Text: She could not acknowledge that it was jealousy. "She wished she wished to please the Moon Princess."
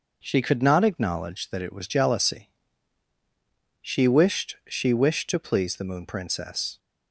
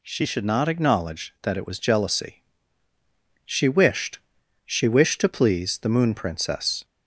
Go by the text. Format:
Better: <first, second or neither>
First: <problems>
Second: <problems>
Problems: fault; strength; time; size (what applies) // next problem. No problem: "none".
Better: first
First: none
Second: says "should" for "could"; at 0.2 s // pauses between "wished" and "she"; noticeable; at 4.1 s; 0.46 s long